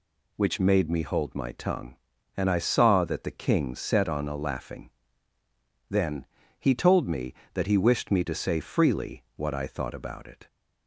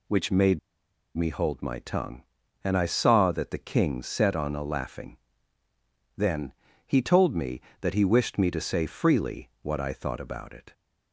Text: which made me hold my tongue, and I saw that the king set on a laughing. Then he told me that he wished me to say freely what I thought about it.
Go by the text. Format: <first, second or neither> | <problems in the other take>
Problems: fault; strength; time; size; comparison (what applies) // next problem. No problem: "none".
first | pauses between "made" and "me"; noticeable; at 0.5 s; 0.57 s long // pauses between "Then" and "he"; slight; at 6.5 s; 0.34 s long; slight in the first